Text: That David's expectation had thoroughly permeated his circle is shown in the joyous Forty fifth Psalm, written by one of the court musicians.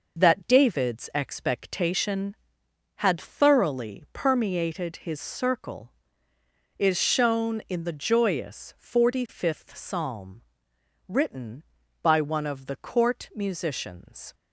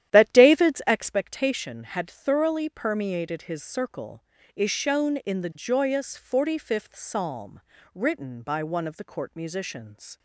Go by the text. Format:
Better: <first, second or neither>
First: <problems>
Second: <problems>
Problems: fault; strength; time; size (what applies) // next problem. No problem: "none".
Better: first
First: none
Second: starts louder than the rest; strong; until 1.2 s; 11.5 dB